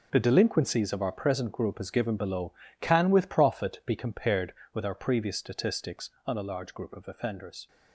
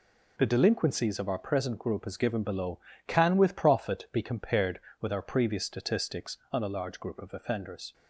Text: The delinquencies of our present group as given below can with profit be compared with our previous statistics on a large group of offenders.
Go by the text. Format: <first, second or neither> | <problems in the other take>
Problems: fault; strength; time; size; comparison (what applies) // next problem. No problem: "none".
second | gets quieter; strong; throughout; 12.5 dB